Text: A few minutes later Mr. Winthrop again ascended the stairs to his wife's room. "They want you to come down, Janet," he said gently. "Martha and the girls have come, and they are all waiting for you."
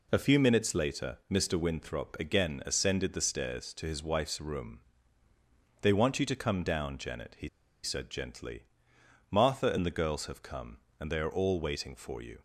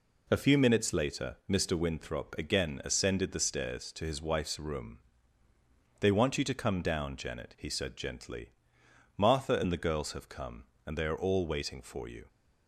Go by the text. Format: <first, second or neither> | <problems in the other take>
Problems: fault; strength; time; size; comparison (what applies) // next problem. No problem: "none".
second | pauses between "he" and "said"; slight; at 7.4 s; 0.35 s long